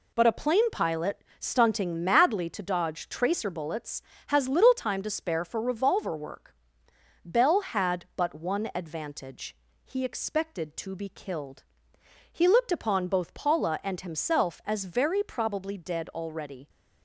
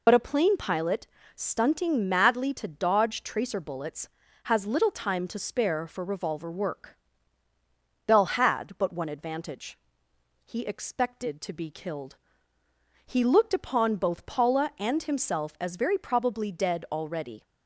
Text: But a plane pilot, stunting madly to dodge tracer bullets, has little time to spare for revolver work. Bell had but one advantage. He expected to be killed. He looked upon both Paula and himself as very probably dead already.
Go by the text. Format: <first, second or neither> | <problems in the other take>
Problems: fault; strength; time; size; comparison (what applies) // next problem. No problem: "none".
first | loses the start of "But"; at 0.0 s; 45 ms